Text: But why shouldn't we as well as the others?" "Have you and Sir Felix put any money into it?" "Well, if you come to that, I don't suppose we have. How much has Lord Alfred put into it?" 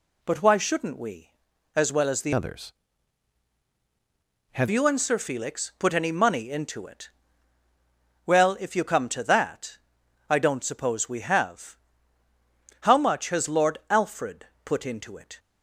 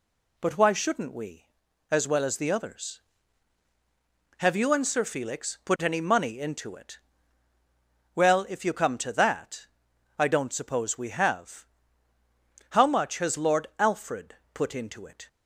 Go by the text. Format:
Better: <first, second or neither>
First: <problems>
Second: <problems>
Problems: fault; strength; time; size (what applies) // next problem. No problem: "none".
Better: second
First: changes voice from "others" to "Have"; from 2.3 to 4.6 s; 2.3 s long // pauses between "Alfred" and "put"; slight; at 14.4 s; 0.18 s long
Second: pauses between "Alfred" and "put"; slight; at 14.3 s; 0.18 s long